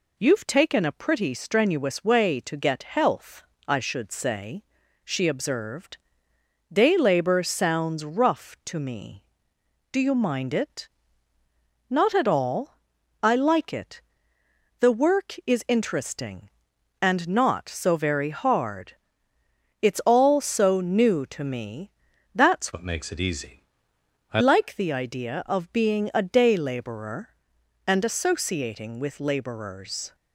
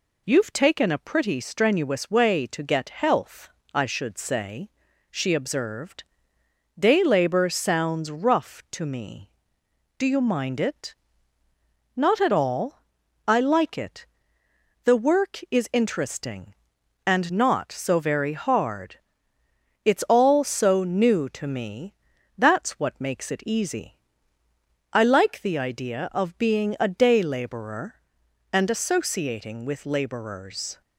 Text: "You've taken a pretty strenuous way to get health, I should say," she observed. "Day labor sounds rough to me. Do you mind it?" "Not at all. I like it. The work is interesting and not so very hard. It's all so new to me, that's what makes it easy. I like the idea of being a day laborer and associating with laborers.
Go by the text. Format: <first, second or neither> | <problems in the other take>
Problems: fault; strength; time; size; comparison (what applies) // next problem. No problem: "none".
second | changes voice from "what" to "I"; from 22.7 to 24.4 s; 1.7 s long